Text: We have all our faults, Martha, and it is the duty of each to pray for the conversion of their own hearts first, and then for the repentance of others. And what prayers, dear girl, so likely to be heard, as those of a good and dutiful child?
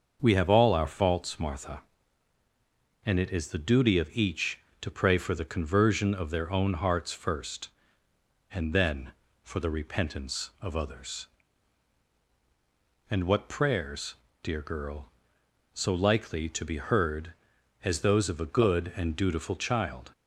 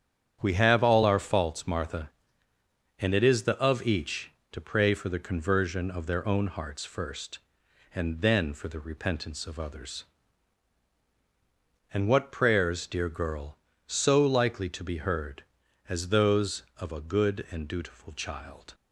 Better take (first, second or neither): first